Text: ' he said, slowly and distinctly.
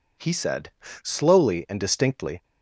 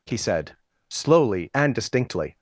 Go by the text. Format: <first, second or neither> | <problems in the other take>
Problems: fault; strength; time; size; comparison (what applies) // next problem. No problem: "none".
neither | none